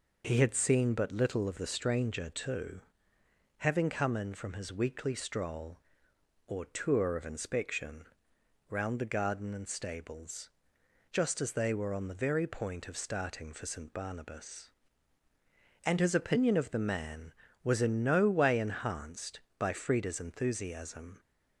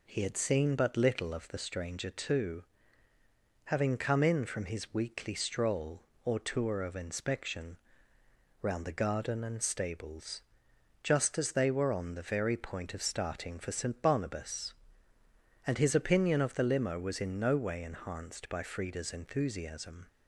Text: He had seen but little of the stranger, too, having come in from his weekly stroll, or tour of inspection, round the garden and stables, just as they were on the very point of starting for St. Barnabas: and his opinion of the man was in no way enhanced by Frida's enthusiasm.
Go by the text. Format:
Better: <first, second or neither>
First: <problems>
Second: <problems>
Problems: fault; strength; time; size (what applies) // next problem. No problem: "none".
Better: first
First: none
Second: says "limo" for "man"; at 16.6 s